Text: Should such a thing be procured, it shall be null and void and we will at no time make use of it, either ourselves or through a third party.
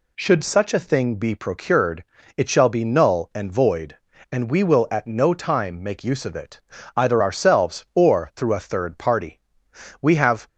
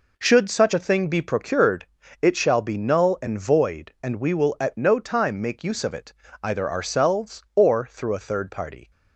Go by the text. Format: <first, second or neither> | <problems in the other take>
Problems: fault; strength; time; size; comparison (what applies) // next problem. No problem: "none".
second | goes on to say "We have"; slight; from 10.0 s on; 0.44 s long